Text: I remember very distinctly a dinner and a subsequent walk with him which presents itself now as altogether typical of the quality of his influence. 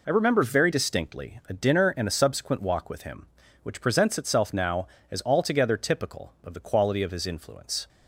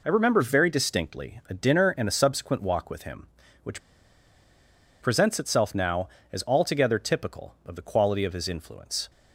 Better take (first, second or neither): first